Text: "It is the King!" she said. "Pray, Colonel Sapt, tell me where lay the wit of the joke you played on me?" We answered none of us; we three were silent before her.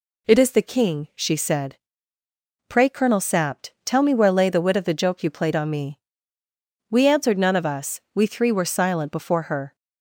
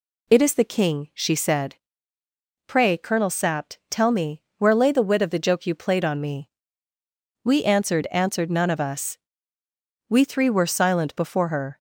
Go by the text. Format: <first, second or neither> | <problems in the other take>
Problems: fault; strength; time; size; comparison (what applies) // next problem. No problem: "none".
first | pauses between "me" and "where"; slight; at 4.4 s; 0.16 s long // says "answered" twice; at 8.1 s